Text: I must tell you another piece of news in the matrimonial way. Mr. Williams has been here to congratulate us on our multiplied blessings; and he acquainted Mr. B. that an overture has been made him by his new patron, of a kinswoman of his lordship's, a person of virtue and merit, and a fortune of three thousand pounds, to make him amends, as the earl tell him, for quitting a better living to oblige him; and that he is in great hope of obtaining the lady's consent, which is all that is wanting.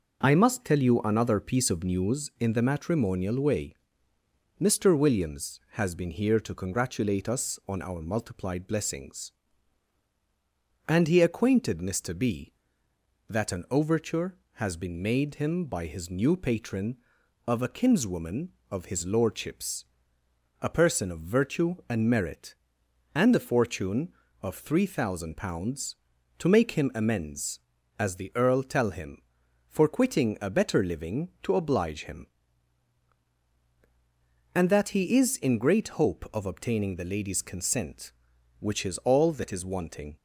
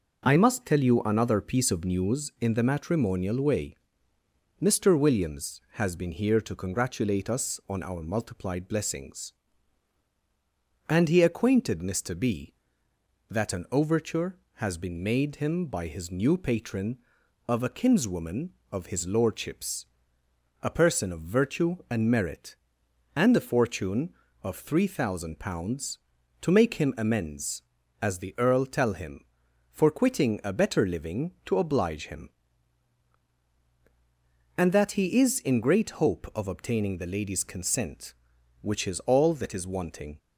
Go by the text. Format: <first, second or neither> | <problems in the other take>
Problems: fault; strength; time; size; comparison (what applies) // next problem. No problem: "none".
neither | none